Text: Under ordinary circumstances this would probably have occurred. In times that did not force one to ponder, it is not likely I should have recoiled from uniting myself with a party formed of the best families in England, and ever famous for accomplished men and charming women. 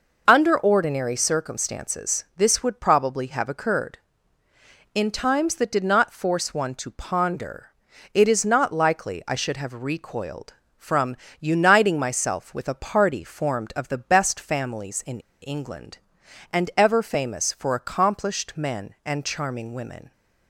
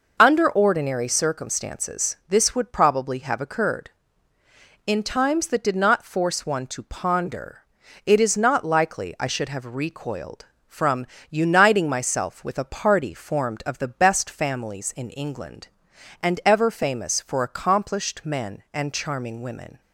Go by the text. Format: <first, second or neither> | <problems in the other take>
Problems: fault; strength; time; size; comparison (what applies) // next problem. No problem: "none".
second | pauses between "from" and "uniting"; slight; at 11.1 s; 0.24 s long; slight in the second // pauses between "in" and "England"; slight; at 15.1 s; 0.22 s long